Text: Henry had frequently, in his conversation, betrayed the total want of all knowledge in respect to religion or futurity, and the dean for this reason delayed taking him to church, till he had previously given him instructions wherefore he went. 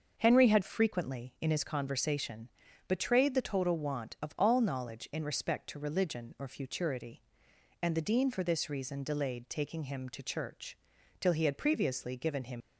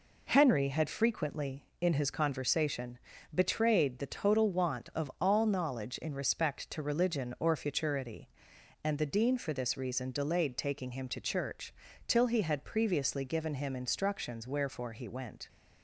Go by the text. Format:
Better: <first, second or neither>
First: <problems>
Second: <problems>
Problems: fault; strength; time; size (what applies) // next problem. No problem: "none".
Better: second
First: starts louder than the rest; until 1.1 s; 6.5 dB // stops before "instructions wherefore he went"; at 12.6 s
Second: none